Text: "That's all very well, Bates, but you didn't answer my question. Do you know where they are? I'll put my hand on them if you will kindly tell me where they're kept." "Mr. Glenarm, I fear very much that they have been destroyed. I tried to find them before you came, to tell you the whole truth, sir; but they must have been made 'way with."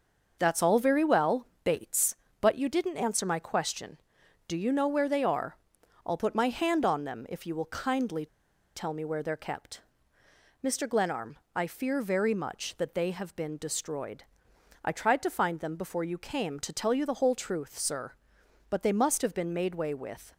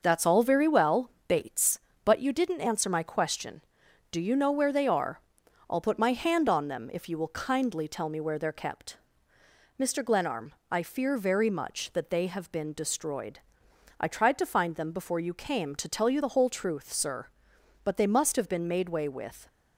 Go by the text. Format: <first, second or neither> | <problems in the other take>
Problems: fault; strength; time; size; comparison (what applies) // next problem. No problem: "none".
second | pauses between "kindly" and "tell"; noticeable; at 8.2 s; 0.49 s long